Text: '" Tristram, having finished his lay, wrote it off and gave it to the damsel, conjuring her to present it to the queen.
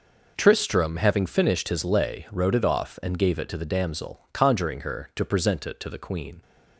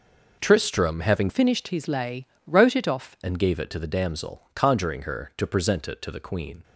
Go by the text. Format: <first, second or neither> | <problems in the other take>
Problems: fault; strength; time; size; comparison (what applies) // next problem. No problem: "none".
first | changes voice from "finished" to "off"; from 1.2 to 3.1 s; 1.9 s long